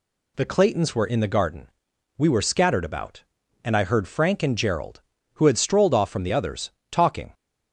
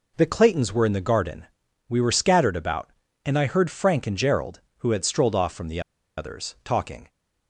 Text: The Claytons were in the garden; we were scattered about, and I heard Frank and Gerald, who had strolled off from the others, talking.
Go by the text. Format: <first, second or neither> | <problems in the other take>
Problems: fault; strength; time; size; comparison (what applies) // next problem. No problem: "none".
first | pauses between "the" and "others"; at 5.7 s; 0.37 s long